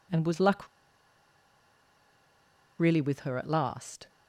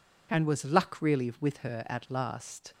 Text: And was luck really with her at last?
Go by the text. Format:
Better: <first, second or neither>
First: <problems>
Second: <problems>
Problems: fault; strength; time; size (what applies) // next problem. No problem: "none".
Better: second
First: pauses between "luck" and "really"; strong; at 0.6 s; 2.1 s long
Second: none